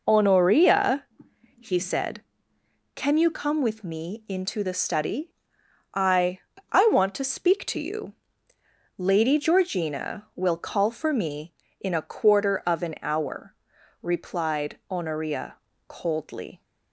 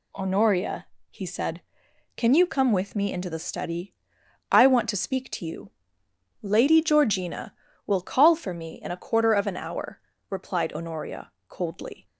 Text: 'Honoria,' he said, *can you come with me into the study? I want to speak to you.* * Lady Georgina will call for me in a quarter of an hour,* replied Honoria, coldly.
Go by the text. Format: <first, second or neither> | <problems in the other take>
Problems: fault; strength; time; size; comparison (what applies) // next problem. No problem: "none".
second | says "I" twice; at 6.7 s